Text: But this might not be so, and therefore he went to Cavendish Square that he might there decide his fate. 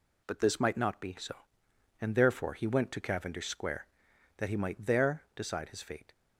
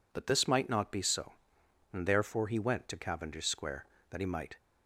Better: first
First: none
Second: stops before "there decide his fate"; at 4.5 s

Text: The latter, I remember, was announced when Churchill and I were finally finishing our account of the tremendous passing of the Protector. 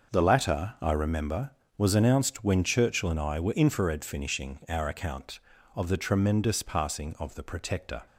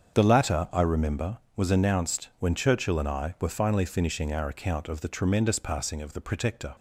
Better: second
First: starts louder than the rest; noticeable; until 1.1 s; 6 dB // says "infrared" for "finally"; at 3.5 s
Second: starts louder than the rest; strong; until 1.2 s; 7.5 dB

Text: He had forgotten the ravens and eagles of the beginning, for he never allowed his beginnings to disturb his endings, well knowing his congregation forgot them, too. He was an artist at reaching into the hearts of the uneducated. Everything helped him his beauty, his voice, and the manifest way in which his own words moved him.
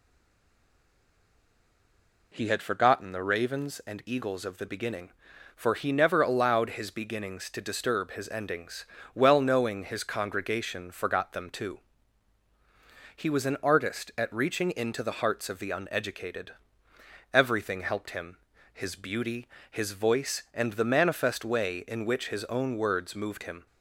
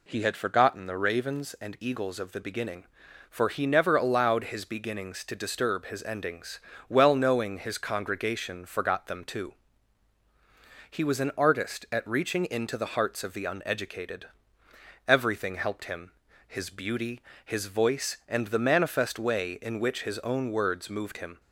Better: second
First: stays silent before the first word; until 2.3 s; 2.3 s long // pauses between "him" and "his"; slight; at 18.3 s; 0.36 s long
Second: pauses between "him" and "his"; slight; at 16.1 s; 0.36 s long

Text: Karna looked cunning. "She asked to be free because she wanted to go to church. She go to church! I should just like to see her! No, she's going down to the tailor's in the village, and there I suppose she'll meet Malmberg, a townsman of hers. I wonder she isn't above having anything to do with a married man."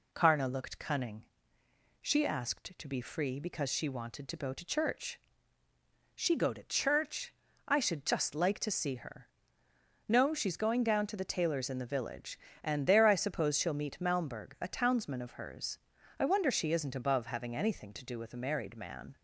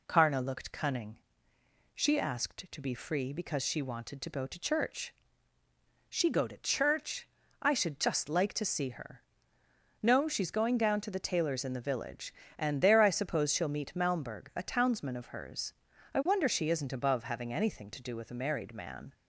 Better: neither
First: none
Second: none

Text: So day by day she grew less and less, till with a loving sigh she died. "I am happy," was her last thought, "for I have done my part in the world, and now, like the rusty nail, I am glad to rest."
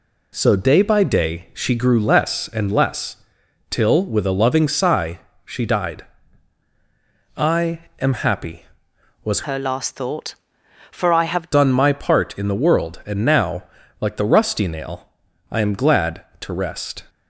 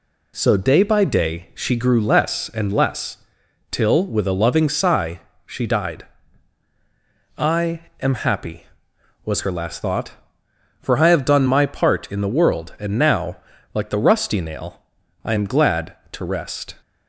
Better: second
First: pauses between "sigh" and "she"; slight; at 5.1 s; 0.26 s long // pauses between "I" and "am"; slight; at 7.8 s; 0.20 s long // changes voice from "her" to "have"; from 9.4 to 11.5 s; 2.1 s long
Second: pauses between "sigh" and "she"; slight; at 5.2 s; 0.26 s long // pauses between "I" and "am"; slight; at 7.8 s; 0.20 s long

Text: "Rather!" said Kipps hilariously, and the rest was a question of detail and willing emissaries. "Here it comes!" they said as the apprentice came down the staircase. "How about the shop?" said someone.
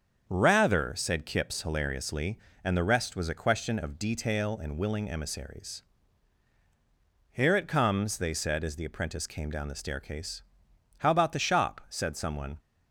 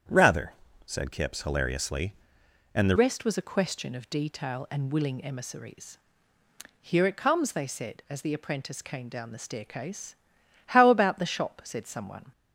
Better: first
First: starts louder than the rest; until 1.2 s; 7 dB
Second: starts louder than the rest; strong; until 1.4 s; 8.5 dB // changes voice at "rest"; from 2.9 s on; 9.4 s long

